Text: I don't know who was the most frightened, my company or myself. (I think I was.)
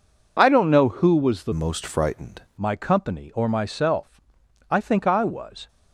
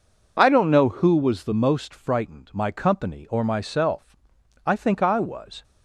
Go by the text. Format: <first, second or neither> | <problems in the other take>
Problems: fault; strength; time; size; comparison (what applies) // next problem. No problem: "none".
second | changes voice from "most" to "frightened"; from 1.5 to 2.4 s; 0.9 s long